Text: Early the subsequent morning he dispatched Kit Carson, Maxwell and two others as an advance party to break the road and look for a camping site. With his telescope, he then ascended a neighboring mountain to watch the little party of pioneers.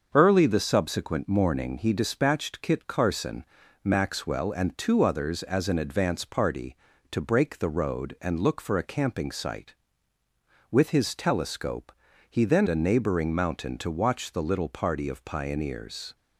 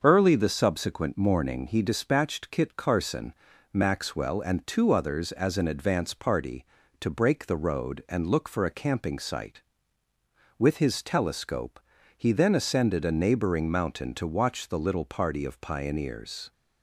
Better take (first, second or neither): second